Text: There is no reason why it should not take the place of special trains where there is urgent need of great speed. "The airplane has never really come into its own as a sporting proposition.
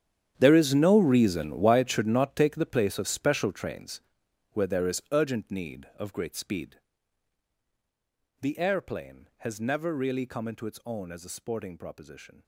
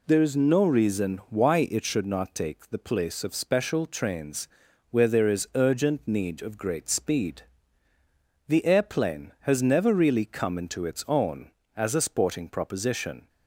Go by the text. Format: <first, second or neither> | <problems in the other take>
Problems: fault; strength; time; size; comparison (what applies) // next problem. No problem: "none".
second | gets quieter; strong; throughout; 16 dB // pauses between "trains" and "where"; noticeable; at 4.0 s; 0.50 s long; also in the second